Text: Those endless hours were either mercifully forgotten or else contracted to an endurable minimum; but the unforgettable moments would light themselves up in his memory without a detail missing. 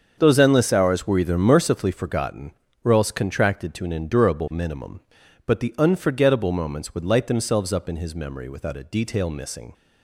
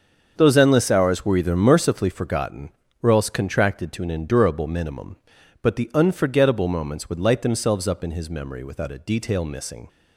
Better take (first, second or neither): neither